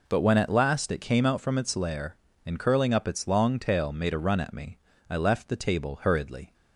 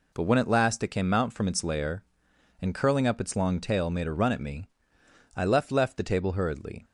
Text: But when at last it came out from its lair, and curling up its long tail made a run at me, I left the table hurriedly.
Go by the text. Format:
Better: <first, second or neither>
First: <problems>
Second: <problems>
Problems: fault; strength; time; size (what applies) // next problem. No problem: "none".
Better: first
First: none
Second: says "left" twice; at 5.7 s